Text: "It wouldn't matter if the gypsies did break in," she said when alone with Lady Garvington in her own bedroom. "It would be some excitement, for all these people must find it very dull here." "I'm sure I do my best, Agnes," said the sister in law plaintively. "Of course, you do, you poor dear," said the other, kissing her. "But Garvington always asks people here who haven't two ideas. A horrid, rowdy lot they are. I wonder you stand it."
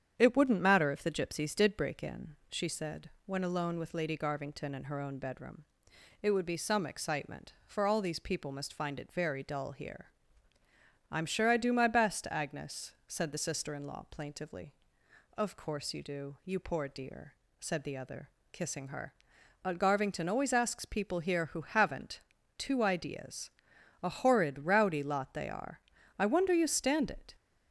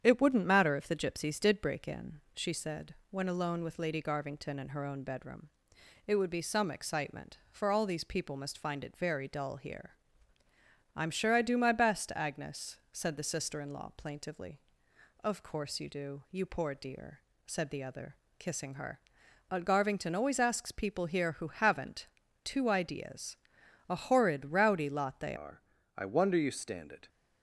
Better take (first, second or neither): first